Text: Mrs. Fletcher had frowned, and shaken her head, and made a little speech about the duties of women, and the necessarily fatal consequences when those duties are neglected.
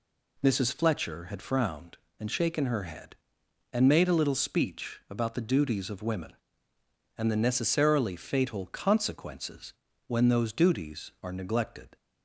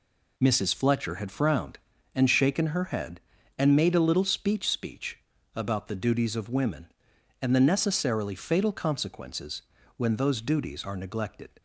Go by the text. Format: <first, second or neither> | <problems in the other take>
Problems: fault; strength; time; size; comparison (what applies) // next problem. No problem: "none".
first | says "speech" twice; at 4.6 s // pauses between "consequences" and "when"; slight; at 9.6 s; 0.34 s long; slight in the first